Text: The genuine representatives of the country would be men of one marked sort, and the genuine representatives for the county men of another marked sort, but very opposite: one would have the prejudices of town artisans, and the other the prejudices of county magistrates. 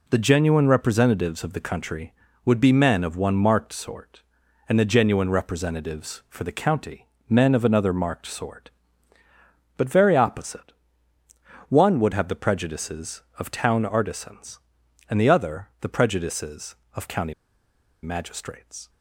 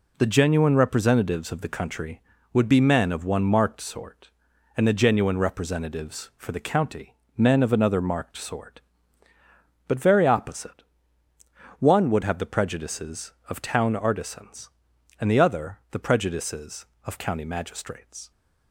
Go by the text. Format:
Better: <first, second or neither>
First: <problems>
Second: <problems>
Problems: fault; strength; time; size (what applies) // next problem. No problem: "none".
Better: second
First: pauses between "county" and "men"; slight; at 7.0 s; 0.20 s long // pauses between "county" and "magistrates"; noticeable; at 17.3 s; 0.69 s long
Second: pauses between "county" and "men"; slight; at 7.1 s; 0.20 s long